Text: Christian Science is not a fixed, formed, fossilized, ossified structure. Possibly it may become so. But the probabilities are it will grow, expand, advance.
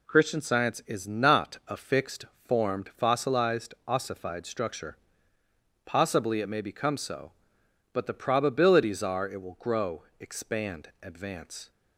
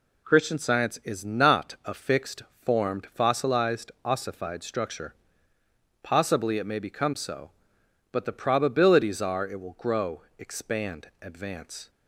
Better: neither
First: none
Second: none

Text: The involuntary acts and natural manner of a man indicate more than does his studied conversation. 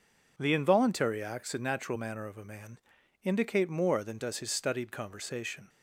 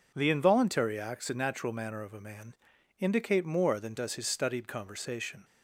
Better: neither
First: pauses between "man" and "indicate"; at 2.7 s; 0.44 s long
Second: pauses between "man" and "indicate"; at 2.5 s; 0.44 s long

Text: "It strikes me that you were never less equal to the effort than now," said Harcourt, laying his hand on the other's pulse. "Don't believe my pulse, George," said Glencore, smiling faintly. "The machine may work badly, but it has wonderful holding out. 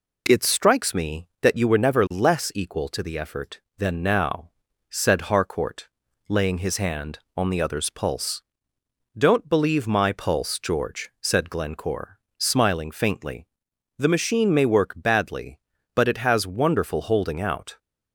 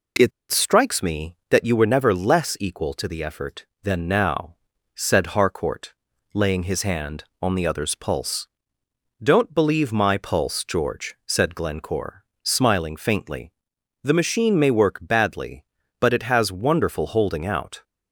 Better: first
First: none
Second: pauses between "It" and "strikes"; slight; at 0.3 s; 0.20 s long

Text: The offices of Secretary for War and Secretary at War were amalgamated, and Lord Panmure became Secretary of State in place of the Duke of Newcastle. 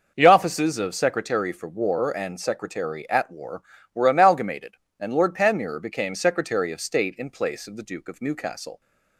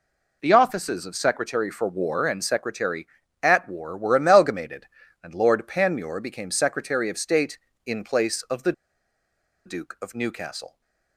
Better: first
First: none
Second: pauses between "the" and "Duke"; noticeable; at 8.7 s; 0.93 s long

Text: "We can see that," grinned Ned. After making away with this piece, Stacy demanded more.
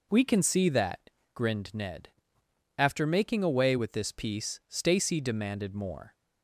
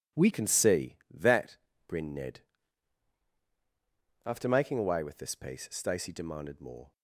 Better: first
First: none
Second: changes voice at "can"; from 0.3 s on; 6.6 s long

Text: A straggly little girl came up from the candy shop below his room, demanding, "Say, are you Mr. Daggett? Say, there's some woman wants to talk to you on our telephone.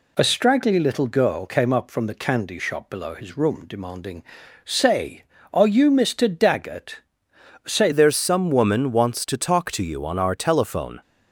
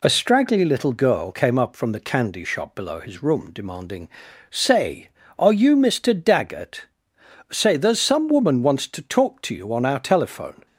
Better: second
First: changes voice at "there's"; from 7.9 s on; 3.1 s long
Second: none

